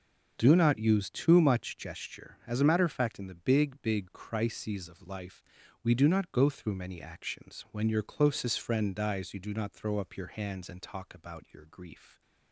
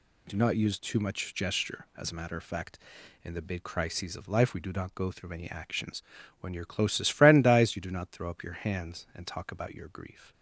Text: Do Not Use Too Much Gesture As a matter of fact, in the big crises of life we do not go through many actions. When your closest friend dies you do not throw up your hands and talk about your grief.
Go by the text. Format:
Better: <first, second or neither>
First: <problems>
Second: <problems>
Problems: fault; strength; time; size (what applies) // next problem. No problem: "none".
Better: second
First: starts louder than the rest; noticeable; until 1.3 s; 6 dB // says "big" twice; at 3.8 s // pauses between "life" and "we"; at 5.4 s; 0.42 s long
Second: none